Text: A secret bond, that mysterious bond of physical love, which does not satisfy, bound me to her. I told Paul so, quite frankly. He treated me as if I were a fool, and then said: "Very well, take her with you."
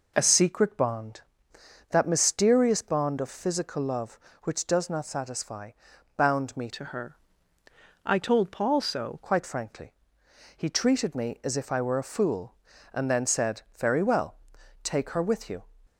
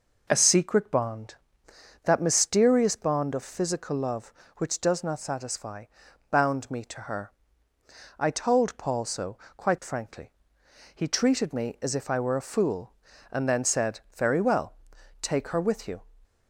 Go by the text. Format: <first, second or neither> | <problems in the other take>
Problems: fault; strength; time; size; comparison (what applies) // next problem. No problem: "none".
second | changes voice from "to" to "so"; from 6.7 to 9.1 s; 2.4 s long